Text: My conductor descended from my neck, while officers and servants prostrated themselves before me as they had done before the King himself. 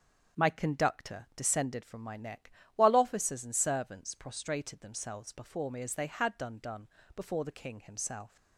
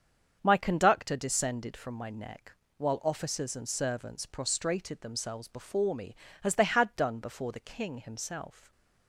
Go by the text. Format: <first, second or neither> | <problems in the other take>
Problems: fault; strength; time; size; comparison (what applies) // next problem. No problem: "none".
second | starts louder than the rest; until 1.4 s; 6.5 dB; also in the second // says "done" twice; at 6.6 s